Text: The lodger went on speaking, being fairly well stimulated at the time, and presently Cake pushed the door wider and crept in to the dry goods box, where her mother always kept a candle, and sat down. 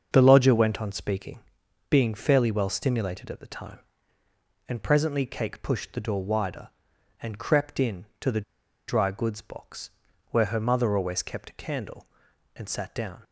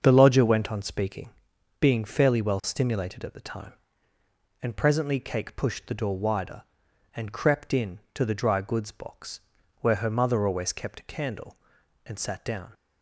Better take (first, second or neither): second